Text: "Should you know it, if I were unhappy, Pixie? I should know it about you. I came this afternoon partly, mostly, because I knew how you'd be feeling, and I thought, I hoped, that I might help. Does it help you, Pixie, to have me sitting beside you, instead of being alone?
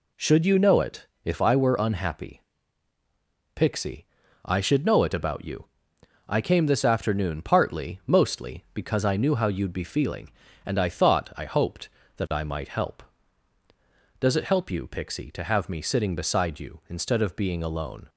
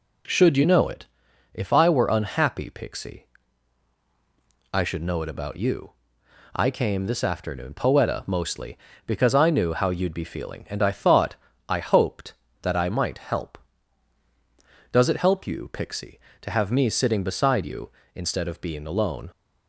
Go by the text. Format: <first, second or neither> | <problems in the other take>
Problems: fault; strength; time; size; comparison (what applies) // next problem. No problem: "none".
first | says "poeta" for "partly"; at 7.7 s